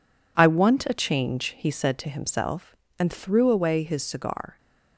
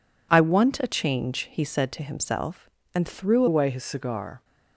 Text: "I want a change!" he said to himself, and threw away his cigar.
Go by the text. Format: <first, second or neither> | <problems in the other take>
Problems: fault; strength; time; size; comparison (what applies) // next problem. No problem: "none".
first | changes voice at "away"; from 3.4 s on; 1.0 s long